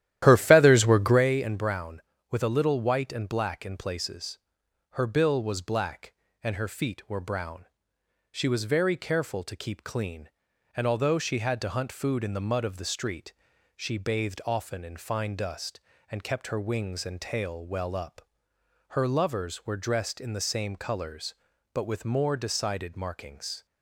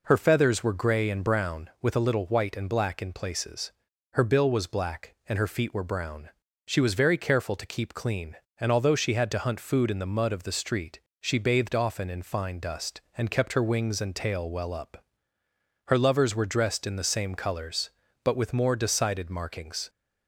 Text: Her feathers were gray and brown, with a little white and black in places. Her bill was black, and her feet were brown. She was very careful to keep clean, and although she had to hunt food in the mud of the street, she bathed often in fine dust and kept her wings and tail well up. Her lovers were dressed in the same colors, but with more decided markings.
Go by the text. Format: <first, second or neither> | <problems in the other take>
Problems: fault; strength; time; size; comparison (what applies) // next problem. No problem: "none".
second | starts louder than the rest; strong; until 1.3 s; 12.5 dB